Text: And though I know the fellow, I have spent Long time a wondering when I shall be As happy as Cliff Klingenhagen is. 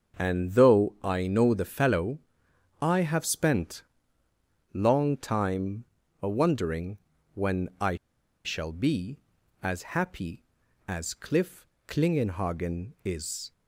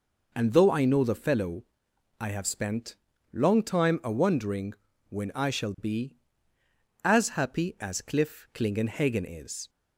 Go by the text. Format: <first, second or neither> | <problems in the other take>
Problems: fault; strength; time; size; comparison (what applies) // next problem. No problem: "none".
second | starts louder than the rest; until 1.2 s; 6.5 dB // pauses between "spent" and "Long"; noticeable; at 3.8 s; 0.90 s long; slight in the second // pauses between "time" and "a"; slight; at 5.8 s; 0.36 s long // pauses between "wondering" and "when"; at 6.9 s; 0.38 s long; slight in the second // pauses between "I" and "shall"; noticeable; at 7.9 s; 0.49 s long // pauses between "Cliff" and "Klingenhagen"; slight; at 11.6 s; 0.22 s long